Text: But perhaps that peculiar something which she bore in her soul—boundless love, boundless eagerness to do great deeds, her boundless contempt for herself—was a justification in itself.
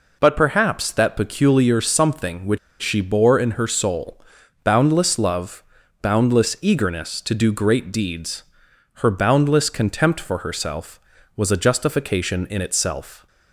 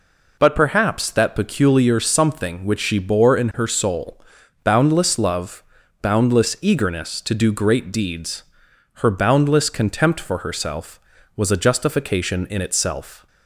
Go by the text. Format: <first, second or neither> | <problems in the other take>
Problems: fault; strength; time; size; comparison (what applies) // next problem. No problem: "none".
second | pauses between "which" and "she"; slight; at 2.5 s; 0.24 s long